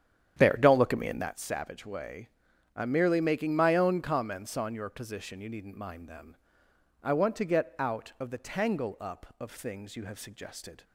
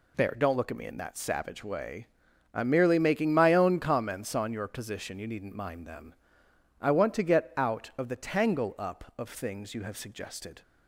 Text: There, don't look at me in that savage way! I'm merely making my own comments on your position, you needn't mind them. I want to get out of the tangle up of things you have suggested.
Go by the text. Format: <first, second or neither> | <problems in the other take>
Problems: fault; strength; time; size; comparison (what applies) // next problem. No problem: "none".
second | starts louder than the rest; strong; until 1.5 s; 9 dB